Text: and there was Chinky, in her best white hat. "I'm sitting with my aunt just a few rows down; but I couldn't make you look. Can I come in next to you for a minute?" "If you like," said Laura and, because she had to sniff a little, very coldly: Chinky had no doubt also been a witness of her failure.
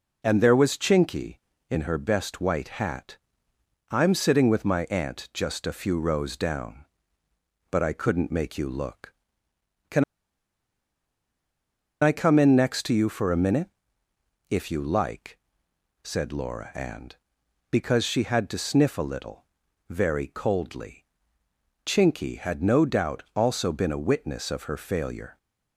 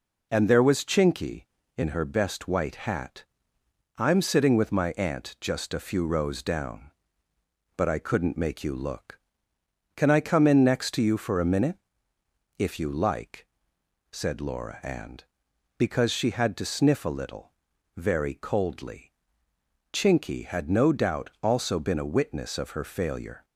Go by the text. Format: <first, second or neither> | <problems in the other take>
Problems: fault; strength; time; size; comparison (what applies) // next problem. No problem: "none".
second | pauses between "Can" and "I"; strong; at 10.0 s; 1.9 s long